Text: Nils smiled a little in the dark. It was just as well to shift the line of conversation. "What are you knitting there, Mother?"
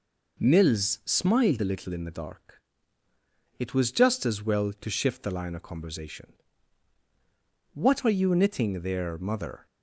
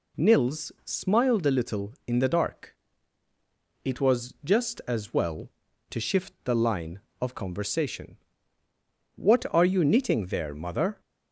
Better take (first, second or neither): neither